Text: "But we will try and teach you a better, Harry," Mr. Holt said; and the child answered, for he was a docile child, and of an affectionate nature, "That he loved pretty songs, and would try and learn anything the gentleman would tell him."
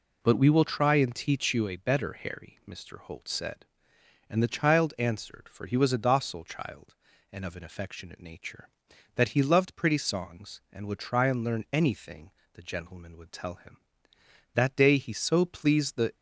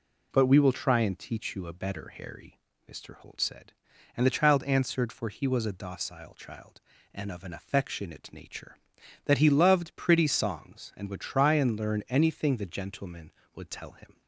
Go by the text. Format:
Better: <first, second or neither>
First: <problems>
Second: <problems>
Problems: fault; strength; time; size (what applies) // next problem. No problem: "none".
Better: second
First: pauses between "anything" and "the"; slight; at 12.3 s; 0.22 s long // goes on to say "That day he so pleased the"; from 14.5 s on; 1.6 s long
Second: none